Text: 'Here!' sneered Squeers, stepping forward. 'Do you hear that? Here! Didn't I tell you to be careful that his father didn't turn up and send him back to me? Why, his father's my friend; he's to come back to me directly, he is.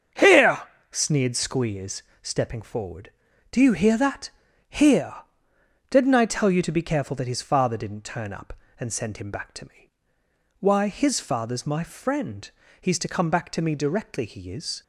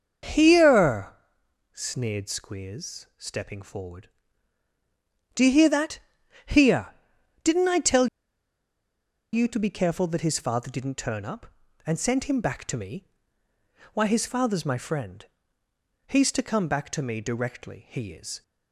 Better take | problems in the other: first | starts louder than the rest; until 1.8 s; 6.5 dB; strong in the first // pauses between "tell" and "you"; strong; at 8.0 s; 1.2 s long

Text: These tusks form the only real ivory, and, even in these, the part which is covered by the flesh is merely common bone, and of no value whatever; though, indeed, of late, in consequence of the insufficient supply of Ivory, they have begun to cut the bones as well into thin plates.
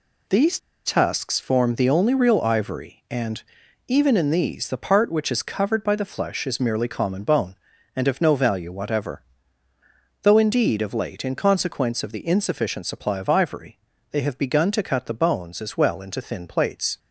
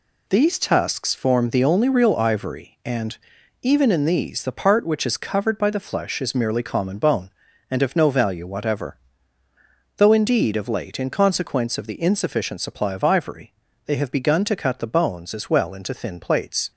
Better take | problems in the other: second | pauses between "These" and "tusks"; slight; at 0.5 s; 0.28 s long

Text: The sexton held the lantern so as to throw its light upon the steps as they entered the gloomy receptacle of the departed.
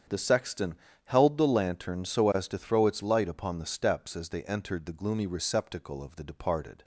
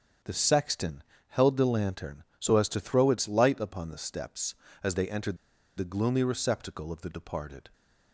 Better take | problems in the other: first | starts louder than the rest; strong; until 1.5 s; 7.5 dB; strong in the first // pauses between "sexton" and "held"; slight; at 1.0 s; 0.26 s long; slight in the first // pauses between "entered" and "the"; at 5.3 s; 0.40 s long

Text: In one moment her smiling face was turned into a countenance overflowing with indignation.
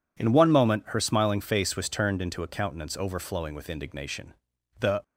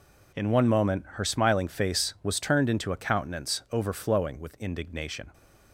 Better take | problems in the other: second | goes on to say "The"; slight; from 4.8 s on; 0.22 s long

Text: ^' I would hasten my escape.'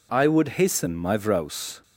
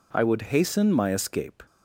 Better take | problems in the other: second | says "vrouws" for "escape"; at 1.1 s

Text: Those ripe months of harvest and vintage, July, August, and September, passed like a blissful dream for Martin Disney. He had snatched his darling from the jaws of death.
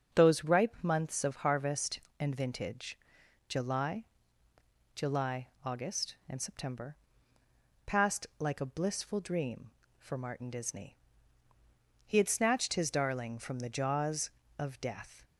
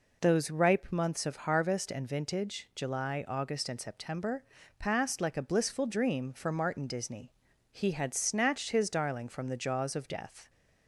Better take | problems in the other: second | starts louder than the rest; until 1.2 s; 7 dB // says "July" twice; at 4.9 s

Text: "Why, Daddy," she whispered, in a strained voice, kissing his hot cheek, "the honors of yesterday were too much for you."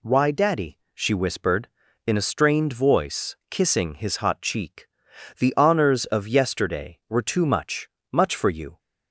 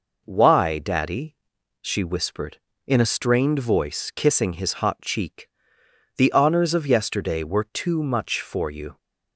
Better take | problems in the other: second | says "much" twice; at 8.0 s

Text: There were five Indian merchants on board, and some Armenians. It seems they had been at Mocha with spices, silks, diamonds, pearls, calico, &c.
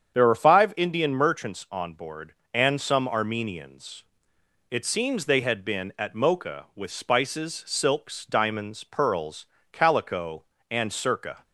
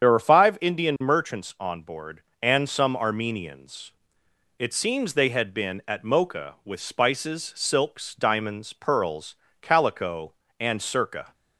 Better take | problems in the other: first | loses the start of "There"; at 0.0 s; 30 ms // starts louder than the rest; strong; until 1.0 s; 8 dB; strong in the first

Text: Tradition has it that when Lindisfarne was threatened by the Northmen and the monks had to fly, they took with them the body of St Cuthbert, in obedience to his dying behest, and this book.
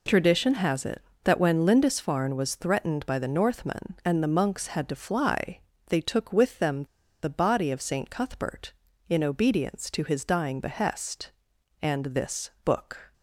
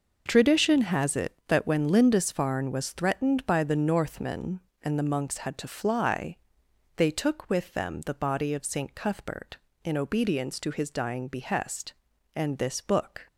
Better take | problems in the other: second | pauses between "them" and "the"; at 6.8 s; 0.37 s long

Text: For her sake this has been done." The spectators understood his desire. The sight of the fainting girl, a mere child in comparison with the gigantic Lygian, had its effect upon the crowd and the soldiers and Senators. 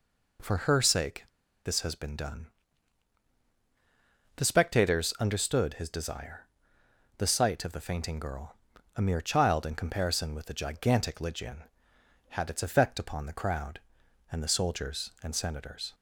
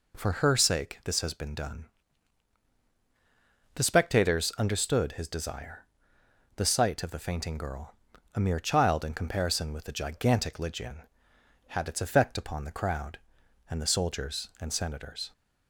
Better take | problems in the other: second | pauses between "sake" and "this"; at 1.2 s; 0.40 s long

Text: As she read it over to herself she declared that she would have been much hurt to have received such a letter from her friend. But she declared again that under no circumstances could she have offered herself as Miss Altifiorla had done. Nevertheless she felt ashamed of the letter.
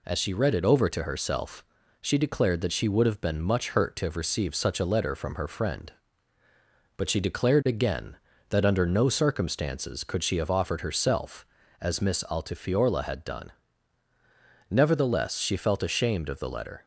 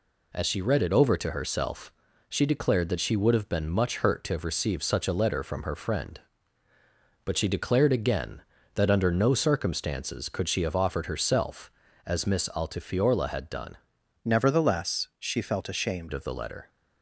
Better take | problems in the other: first | pauses between "herself" and "she"; at 1.9 s; 0.40 s long; also in the first // changes voice from "Nevertheless" to "ashamed"; from 14.2 to 16.1 s; 1.9 s long

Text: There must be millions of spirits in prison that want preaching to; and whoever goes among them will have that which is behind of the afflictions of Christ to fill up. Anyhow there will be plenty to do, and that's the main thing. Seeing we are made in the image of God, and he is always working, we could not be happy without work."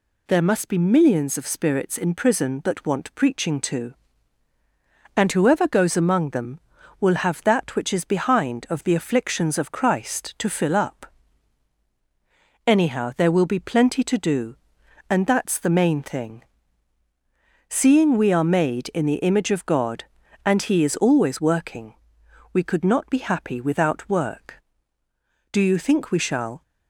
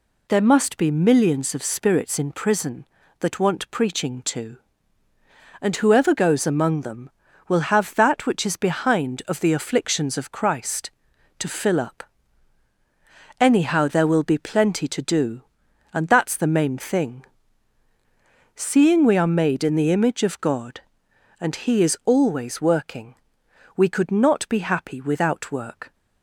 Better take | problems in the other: second | goes on to say "Do you think we shall"; noticeable; from 25.4 s on; 1.1 s long

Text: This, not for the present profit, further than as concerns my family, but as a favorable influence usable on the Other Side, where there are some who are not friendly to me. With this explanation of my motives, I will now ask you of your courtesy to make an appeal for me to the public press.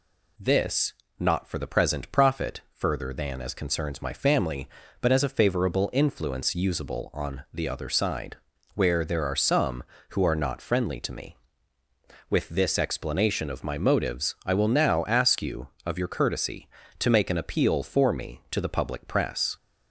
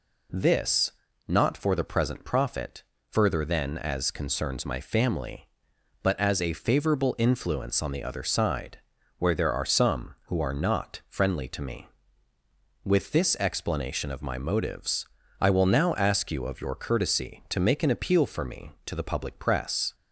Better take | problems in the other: first | skips "usable"; at 7.8 s

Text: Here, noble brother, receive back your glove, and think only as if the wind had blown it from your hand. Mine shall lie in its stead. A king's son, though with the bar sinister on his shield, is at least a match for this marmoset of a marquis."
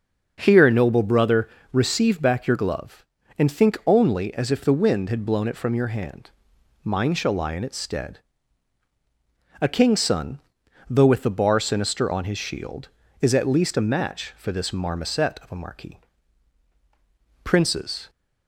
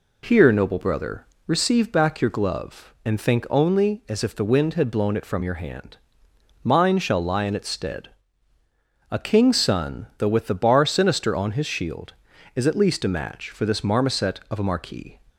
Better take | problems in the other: second | starts louder than the rest; until 1.3 s; 6.5 dB // goes on to say "Princes"; noticeable; from 17.4 s on; 0.68 s long

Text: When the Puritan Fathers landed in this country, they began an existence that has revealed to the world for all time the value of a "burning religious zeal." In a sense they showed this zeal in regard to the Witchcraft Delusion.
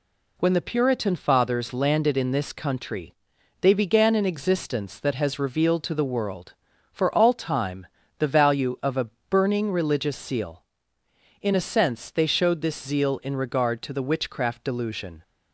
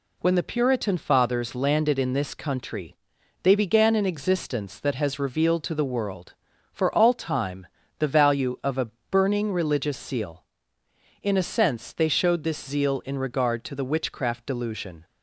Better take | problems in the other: neither | pauses between "time" and "the"; slight; the same in both // pauses between "a" and "burning"; slight; the same in both

